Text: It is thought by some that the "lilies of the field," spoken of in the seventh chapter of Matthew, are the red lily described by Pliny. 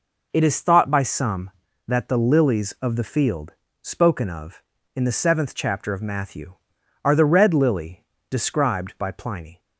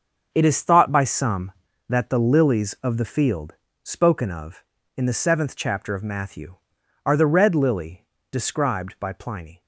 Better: first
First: pauses between "lily" and "described"; slight; at 8.0 s; 0.26 s long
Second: gets quieter; strong; throughout; 10 dB // pauses between "lily" and "described"; slight; at 8.0 s; 0.26 s long

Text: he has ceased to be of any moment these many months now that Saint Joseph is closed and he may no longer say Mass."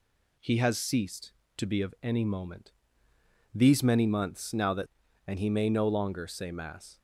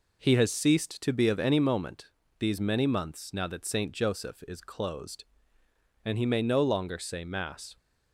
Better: second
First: pauses between "moment" and "these"; noticeable; at 2.7 s; 0.82 s long // skips "Saint Joseph is closed"; at 5.0 s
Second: pauses between "moment" and "these"; slight; at 2.1 s; 0.30 s long

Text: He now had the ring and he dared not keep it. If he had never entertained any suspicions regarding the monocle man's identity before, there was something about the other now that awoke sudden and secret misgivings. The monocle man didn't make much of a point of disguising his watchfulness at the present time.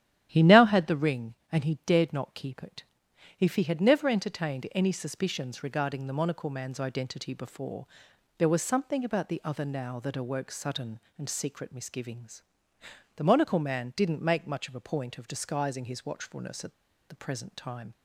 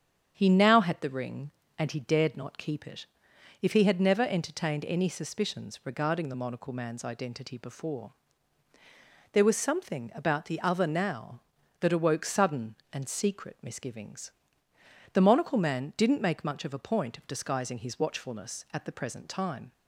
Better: second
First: starts louder than the rest; strong; until 1.3 s; 11.5 dB // pauses between "at" and "the"; slight; at 16.7 s; 0.35 s long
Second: starts louder than the rest; strong; until 1.3 s; 8 dB

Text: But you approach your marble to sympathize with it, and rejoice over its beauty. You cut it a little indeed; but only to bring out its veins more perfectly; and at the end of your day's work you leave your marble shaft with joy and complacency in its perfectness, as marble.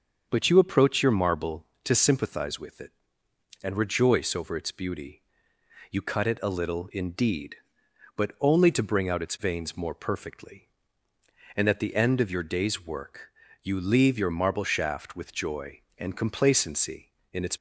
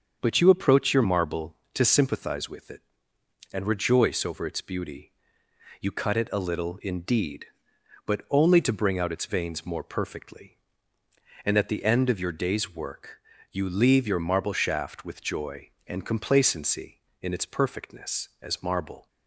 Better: second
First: starts louder than the rest; until 1.2 s; 6.5 dB // pauses between "work" and "you"; slight; at 13.3 s; 0.32 s long // stops before "perfectness as marble"; at 17.5 s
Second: starts louder than the rest; until 1.2 s; 7 dB // pauses between "work" and "you"; slight; at 13.2 s; 0.32 s long

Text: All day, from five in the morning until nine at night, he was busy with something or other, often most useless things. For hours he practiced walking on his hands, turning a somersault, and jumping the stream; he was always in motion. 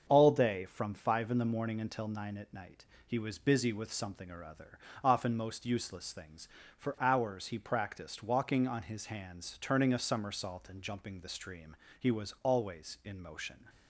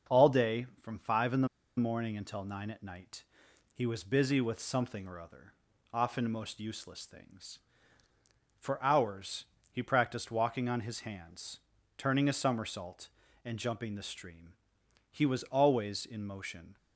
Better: first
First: starts louder than the rest; until 1.1 s; 7 dB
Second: starts louder than the rest; until 1.2 s; 6.5 dB // pauses between "the" and "morning"; slight; at 1.4 s; 0.30 s long // pauses between "hours" and "he"; slight; at 9.4 s; 0.28 s long

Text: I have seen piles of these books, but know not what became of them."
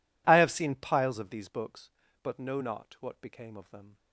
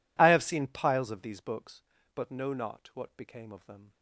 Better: neither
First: none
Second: none

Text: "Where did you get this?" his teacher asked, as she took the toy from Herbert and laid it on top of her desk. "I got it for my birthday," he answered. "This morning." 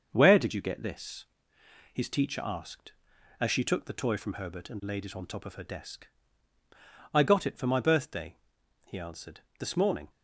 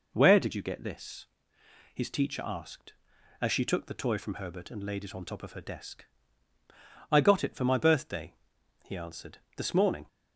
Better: second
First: gets quieter; throughout; 3.5 dB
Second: none

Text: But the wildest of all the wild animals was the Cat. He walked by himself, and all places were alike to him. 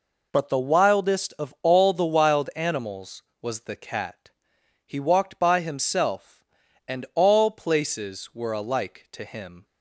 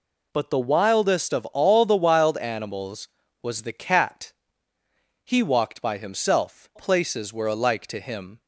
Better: first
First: none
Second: skips "and all"; at 6.7 s

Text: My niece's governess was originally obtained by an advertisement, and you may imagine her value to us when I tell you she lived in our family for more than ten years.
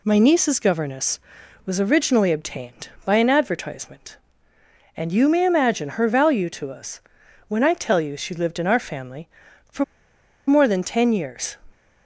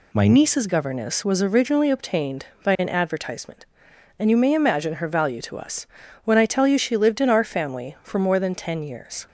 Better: second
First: pauses between "us" and "when"; noticeable; at 6.9 s; 0.48 s long // pauses between "for" and "more"; noticeable; at 9.8 s; 0.63 s long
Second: pauses between "us" and "when"; slight; at 5.8 s; 0.36 s long

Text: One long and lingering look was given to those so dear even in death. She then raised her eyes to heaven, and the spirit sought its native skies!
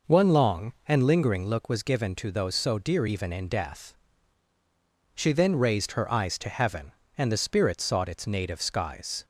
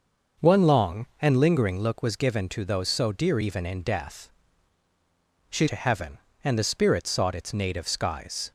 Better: first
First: none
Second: starts louder than the rest; noticeable; until 1.5 s; 6 dB // skips "then raised her eyes"; at 5.6 s

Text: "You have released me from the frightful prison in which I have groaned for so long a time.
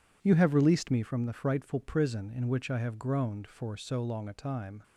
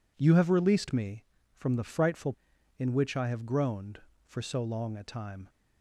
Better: first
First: none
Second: skips "prison"; at 2.5 s

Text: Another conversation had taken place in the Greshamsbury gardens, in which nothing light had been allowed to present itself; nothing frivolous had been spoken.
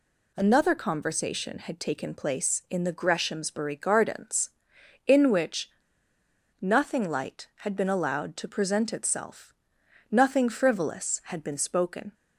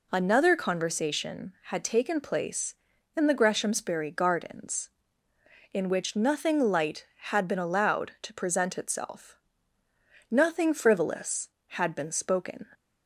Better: second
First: pauses between "which" and "nothing"; noticeable; at 5.6 s; 0.92 s long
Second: none

